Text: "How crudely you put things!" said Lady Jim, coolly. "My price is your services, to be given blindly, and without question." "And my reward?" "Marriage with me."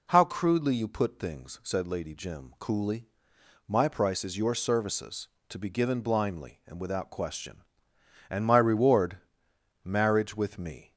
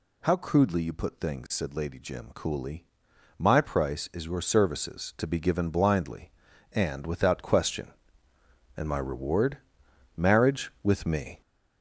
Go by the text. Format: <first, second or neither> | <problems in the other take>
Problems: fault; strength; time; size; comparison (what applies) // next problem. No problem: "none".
first | gets louder; noticeable; throughout; 5.5 dB